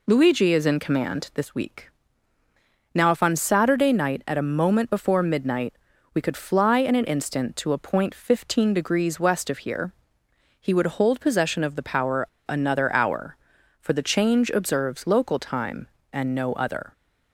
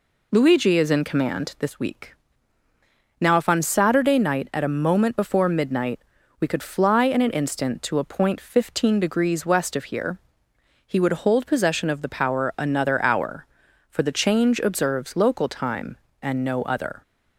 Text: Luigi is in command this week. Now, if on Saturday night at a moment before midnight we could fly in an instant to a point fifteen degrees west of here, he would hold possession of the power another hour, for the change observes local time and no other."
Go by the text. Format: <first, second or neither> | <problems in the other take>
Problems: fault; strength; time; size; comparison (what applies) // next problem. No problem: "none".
second | pauses between "midnight" and "we"; at 5.7 s; 0.40 s long; also in the second // pauses between "power" and "another"; slight; at 12.2 s; 0.22 s long